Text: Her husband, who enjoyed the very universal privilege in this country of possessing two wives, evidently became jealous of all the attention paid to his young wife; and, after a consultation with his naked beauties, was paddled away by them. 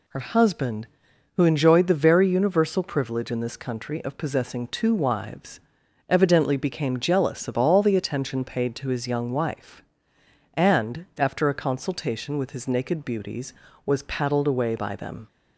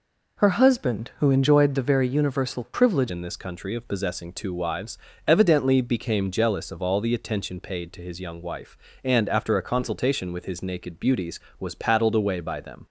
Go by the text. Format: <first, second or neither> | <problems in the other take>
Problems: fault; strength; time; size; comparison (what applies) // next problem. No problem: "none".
first | changes voice at "in"; from 3.0 s on; 9.8 s long